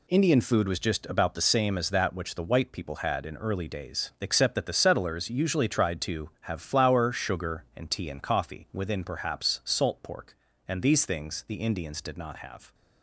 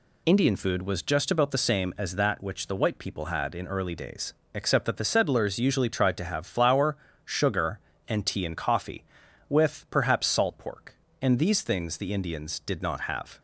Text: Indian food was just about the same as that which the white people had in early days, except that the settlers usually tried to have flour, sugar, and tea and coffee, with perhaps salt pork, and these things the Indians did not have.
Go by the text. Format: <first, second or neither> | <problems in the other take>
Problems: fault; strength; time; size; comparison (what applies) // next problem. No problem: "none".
second | says "within" for "with"; at 8.7 s